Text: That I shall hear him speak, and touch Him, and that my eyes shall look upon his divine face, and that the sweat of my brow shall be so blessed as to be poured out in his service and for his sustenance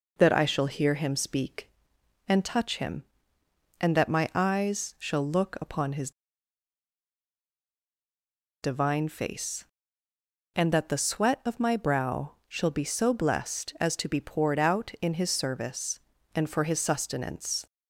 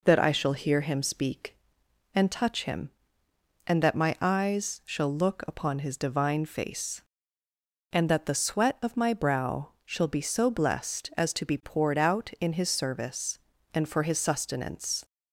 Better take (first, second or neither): second